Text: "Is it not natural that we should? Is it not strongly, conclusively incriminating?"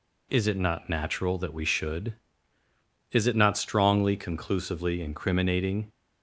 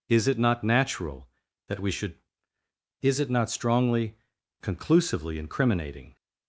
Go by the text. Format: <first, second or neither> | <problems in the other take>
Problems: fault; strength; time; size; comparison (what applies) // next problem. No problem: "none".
neither | none